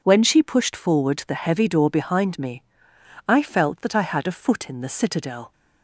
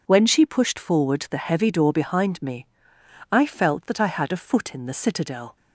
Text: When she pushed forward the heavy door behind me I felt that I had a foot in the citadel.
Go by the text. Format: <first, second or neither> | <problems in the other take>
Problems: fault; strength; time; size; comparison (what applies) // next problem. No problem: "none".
neither | pauses between "me" and "I"; noticeable; the same in both